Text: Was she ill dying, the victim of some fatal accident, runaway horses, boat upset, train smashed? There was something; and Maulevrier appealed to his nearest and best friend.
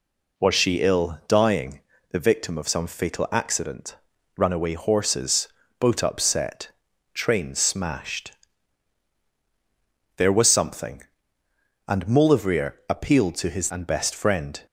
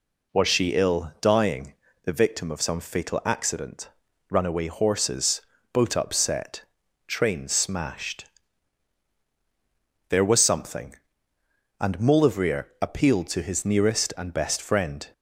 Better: second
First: pauses between "Maulevrier" and "appealed"; slight; at 12.7 s; 0.16 s long // skips "nearest"; at 13.7 s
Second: pauses between "Maulevrier" and "appealed"; slight; at 12.6 s; 0.16 s long

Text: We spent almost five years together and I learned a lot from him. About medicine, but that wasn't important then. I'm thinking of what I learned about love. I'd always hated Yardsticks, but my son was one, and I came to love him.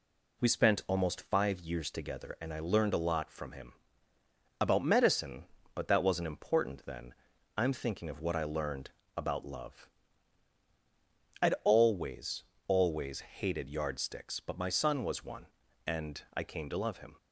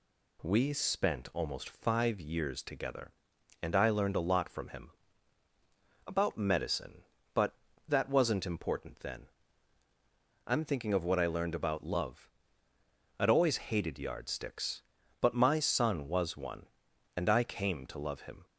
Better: second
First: pauses between "learned" and "about"; slight; at 8.8 s; 0.26 s long // says "always" twice; at 12.6 s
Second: none

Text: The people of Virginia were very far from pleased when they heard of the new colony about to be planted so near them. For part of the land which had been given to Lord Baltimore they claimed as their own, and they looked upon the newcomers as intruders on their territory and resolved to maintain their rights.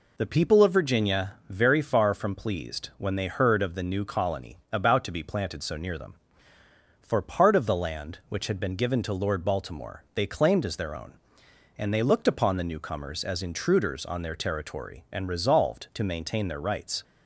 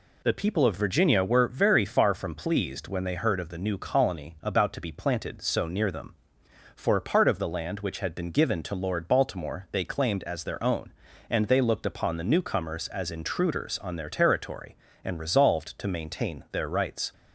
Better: second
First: skips "were"; at 1.4 s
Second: none

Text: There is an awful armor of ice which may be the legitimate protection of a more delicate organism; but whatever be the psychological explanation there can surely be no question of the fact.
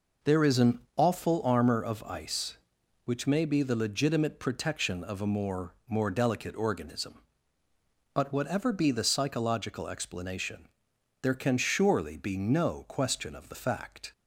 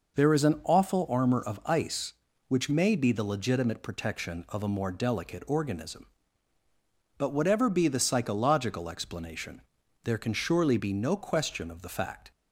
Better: second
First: says "more" twice; at 5.8 s // pauses between "explanation" and "there"; noticeable; at 10.6 s; 0.54 s long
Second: pauses between "explanation" and "there"; at 9.6 s; 0.42 s long

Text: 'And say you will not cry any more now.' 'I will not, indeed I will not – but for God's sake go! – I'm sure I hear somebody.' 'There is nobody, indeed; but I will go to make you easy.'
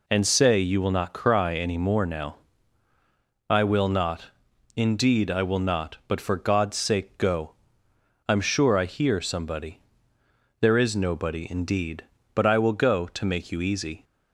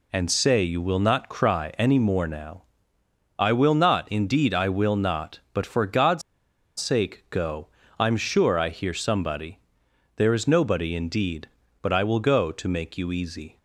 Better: first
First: none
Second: pauses between "God's" and "sake"; noticeable; at 6.2 s; 0.57 s long

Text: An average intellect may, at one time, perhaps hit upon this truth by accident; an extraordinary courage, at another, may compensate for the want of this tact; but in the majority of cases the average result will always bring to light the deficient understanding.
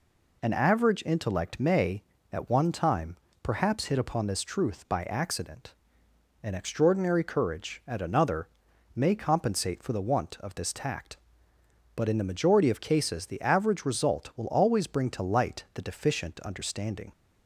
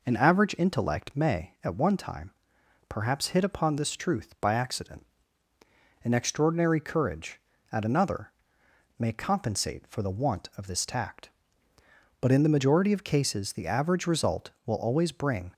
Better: first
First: none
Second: stops before "to light the deficient understanding"; at 15.5 s

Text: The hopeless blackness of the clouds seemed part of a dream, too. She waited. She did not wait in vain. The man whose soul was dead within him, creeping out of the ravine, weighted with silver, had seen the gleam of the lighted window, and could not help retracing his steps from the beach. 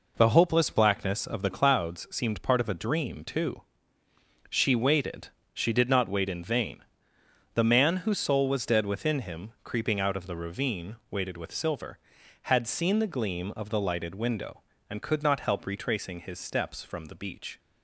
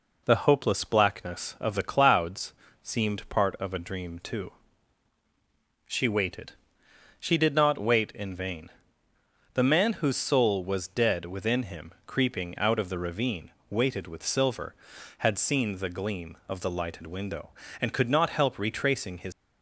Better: first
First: none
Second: pauses between "clouds" and "seemed"; slight; at 2.5 s; 0.30 s long // stops before "steps from the beach"; at 19.3 s

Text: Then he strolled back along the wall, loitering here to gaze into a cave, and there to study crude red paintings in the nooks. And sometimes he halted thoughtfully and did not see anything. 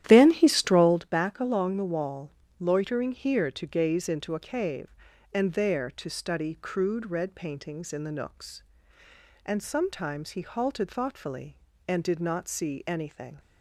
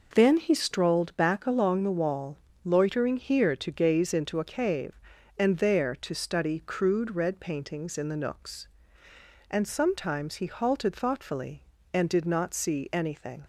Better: second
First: starts louder than the rest; strong; until 1.1 s; 12 dB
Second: none

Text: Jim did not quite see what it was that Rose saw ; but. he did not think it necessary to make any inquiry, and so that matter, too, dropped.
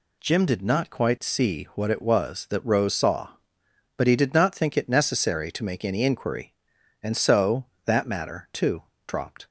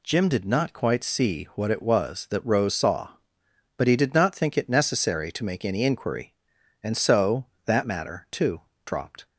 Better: neither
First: none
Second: none

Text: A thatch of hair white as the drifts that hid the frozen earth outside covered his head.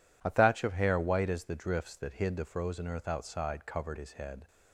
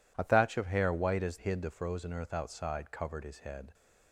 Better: first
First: none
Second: skips "the drifts that"; at 1.3 s

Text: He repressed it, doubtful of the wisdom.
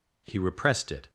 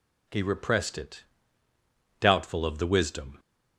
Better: second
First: stops before "doubtful of the wisdom"; at 1.0 s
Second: none

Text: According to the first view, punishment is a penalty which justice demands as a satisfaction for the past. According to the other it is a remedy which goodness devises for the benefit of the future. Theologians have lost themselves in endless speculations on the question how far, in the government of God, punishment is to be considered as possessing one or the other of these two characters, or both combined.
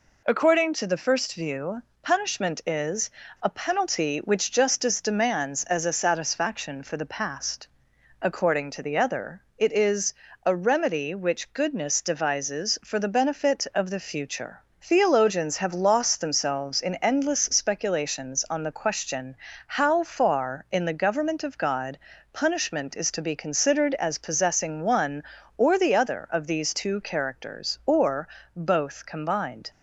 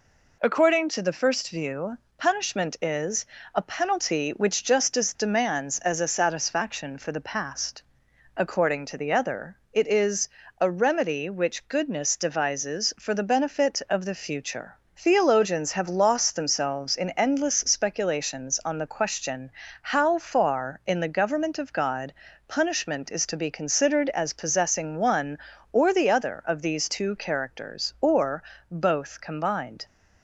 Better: neither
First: pauses between "is" and "a"; slight; at 3.1 s; 0.33 s long // pauses between "other" and "it"; slight; at 9.4 s; 0.16 s long // pauses between "is" and "a"; slight; at 10.1 s; 0.30 s long // pauses between "question" and "how"; slight; at 19.3 s; 0.32 s long // pauses between "or" and "both"; slight; at 28.2 s; 0.30 s long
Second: pauses between "is" and "a"; slight; at 3.2 s; 0.30 s long // pauses between "other" and "it"; slight; at 9.5 s; 0.16 s long // pauses between "is" and "a"; slight; at 10.2 s; 0.30 s long // pauses between "question" and "how"; slight; at 19.5 s; 0.32 s long // pauses between "or" and "both"; slight; at 28.4 s; 0.30 s long

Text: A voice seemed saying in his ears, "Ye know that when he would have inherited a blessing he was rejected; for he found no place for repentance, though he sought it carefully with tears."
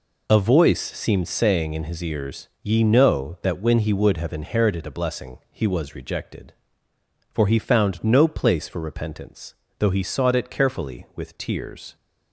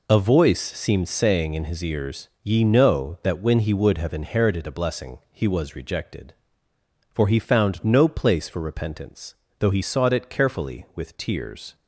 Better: neither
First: none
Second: none

